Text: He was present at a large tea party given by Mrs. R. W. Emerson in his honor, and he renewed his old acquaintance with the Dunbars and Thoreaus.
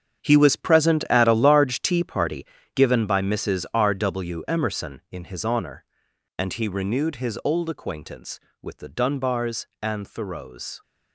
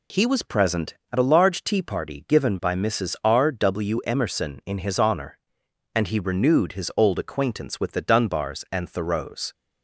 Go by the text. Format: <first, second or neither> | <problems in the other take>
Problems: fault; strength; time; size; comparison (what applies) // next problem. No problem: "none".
second | gets quieter; strong; throughout; 12 dB // pauses between "party" and "given"; slight; at 2.4 s; 0.28 s long